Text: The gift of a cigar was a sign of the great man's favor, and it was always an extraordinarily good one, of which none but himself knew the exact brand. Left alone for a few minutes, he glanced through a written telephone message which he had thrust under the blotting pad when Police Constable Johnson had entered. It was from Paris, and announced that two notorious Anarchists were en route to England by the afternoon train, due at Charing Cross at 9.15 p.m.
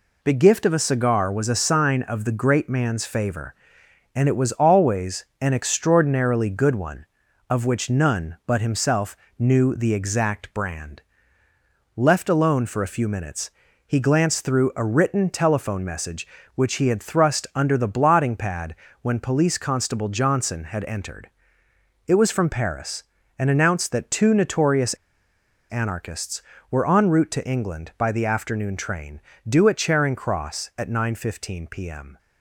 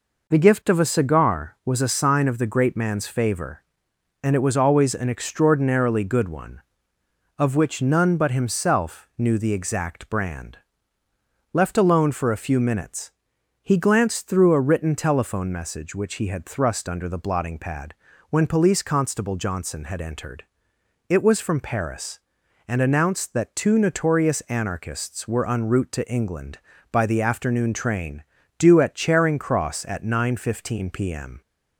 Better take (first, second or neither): second